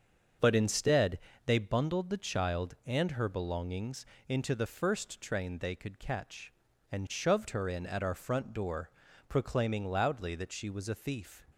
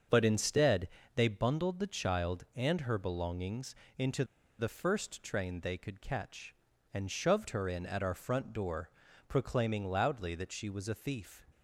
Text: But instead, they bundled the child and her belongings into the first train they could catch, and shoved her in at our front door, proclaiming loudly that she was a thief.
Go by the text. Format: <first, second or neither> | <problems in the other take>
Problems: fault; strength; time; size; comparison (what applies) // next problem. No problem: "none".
first | starts louder than the rest; until 1.3 s; 7 dB; also in the first // pauses between "belongings" and "into"; slight; at 3.7 s; 0.20 s long; slight in the first // pauses between "into" and "the"; slight; at 4.2 s; 0.35 s long